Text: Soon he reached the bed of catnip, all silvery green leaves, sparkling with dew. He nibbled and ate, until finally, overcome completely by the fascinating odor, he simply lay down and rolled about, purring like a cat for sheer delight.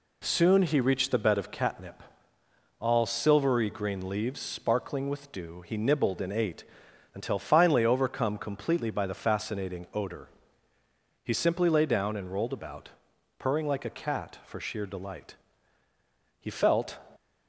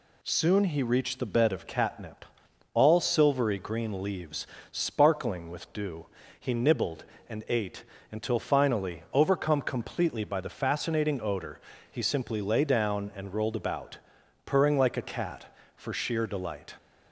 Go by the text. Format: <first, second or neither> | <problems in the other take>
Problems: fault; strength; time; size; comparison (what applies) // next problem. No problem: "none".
second | goes on to say "He felt"; from 16.3 s on; 0.60 s long